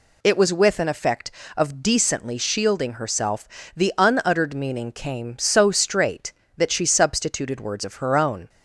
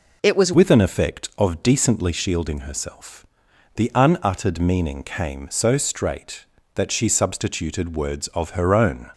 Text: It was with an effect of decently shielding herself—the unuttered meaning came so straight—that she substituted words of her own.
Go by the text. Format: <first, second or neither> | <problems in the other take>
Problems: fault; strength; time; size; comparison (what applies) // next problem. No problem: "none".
first | changes voice at "with"; from 0.5 s on; 8.5 s long